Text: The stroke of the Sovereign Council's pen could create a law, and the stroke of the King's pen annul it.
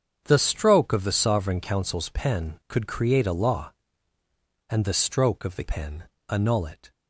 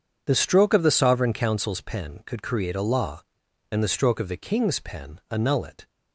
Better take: second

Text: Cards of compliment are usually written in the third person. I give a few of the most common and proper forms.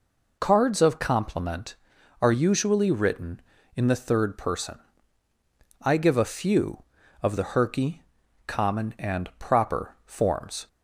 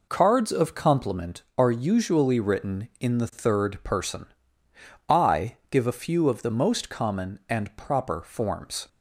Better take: second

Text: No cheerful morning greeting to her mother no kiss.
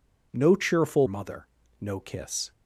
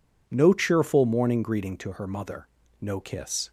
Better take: second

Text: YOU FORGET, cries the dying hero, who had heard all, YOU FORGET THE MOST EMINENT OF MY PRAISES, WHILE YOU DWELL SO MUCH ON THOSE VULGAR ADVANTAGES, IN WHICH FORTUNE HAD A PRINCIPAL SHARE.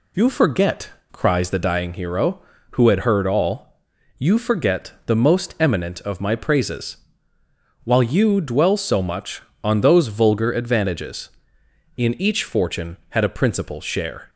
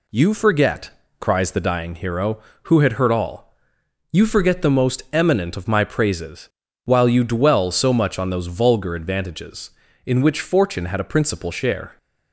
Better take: second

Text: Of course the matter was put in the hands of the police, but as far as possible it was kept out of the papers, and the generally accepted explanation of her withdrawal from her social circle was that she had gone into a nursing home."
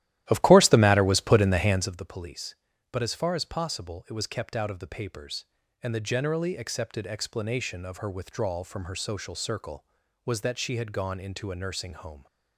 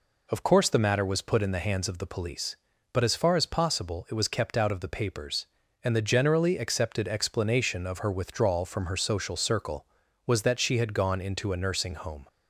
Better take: second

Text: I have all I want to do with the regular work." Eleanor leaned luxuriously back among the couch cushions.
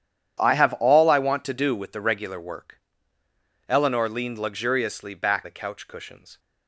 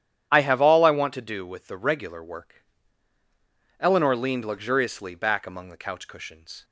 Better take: second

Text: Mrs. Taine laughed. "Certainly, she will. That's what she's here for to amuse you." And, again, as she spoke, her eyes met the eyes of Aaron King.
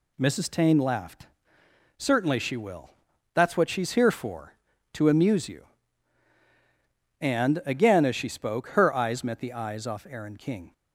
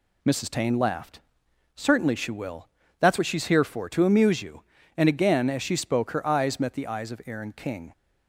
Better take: second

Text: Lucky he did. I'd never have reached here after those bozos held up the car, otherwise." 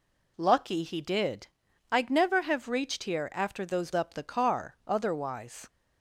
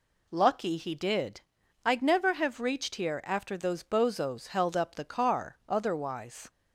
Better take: second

